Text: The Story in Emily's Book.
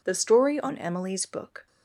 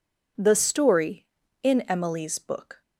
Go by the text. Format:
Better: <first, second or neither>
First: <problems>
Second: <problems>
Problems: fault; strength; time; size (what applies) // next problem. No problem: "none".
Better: second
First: says "on" for "in"; at 0.5 s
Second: none